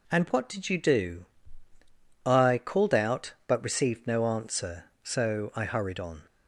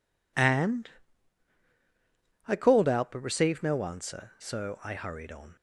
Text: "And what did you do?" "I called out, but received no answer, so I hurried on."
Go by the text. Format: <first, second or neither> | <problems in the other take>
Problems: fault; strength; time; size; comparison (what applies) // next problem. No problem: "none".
first | skips "what did you do"; at 1.6 s